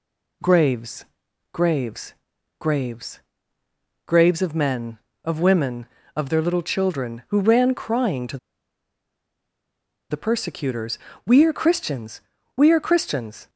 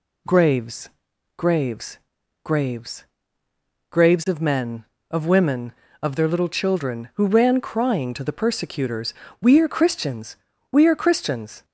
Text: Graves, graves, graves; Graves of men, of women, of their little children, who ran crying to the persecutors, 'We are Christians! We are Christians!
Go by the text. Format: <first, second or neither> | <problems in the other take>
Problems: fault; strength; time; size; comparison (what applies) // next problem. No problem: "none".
second | pauses between "to" and "the"; strong; at 8.3 s; 1.7 s long